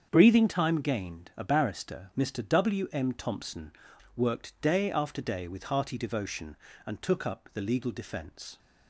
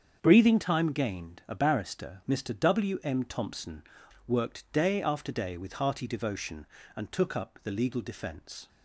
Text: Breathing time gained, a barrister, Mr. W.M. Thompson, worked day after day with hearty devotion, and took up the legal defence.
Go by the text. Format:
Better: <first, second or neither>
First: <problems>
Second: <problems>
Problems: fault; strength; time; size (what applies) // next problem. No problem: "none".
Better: neither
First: starts louder than the rest; strong; until 1.1 s; 7 dB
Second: starts louder than the rest; strong; until 1.2 s; 7 dB